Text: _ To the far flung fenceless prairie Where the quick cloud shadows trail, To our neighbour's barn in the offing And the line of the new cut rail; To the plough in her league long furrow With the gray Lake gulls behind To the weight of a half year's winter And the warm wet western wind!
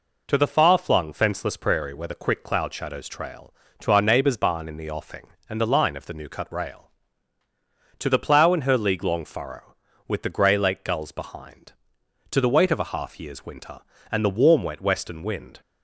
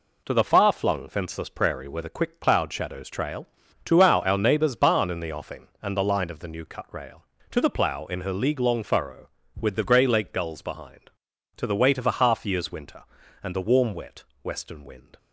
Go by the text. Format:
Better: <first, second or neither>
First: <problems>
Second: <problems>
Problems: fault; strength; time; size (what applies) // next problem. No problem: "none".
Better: first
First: none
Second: says "our" twice; at 4.2 s // pauses between "wet" and "western"; slight; at 14.2 s; 0.20 s long